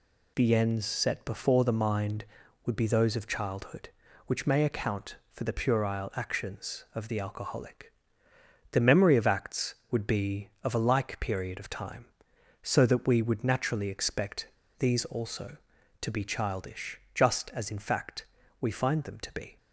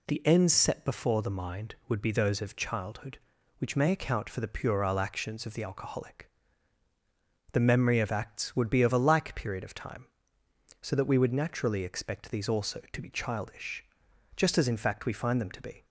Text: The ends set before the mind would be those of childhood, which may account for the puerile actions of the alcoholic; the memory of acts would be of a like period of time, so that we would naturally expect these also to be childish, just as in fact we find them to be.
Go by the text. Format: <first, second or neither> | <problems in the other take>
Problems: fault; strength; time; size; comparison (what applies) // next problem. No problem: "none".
second | pauses between "expect" and "these"; slight; at 14.4 s; 0.31 s long // pauses between "fact" and "we"; slight; at 18.2 s; 0.34 s long